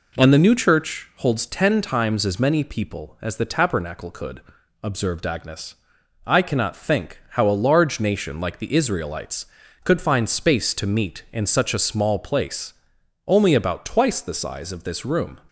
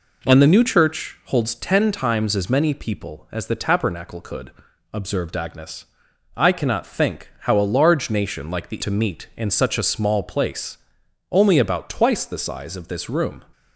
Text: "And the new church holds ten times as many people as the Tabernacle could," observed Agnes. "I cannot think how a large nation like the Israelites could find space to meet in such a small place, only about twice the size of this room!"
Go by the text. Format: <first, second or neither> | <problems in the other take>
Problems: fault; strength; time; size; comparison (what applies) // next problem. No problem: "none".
first | skips "Israelites could find space"; at 8.8 s